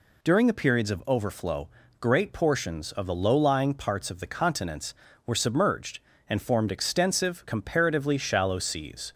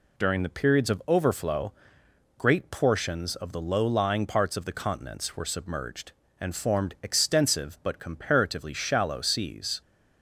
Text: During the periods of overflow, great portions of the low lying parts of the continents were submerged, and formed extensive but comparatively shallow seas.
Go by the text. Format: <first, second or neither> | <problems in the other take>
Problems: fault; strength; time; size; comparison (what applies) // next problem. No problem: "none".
second | skips "but"; at 7.4 s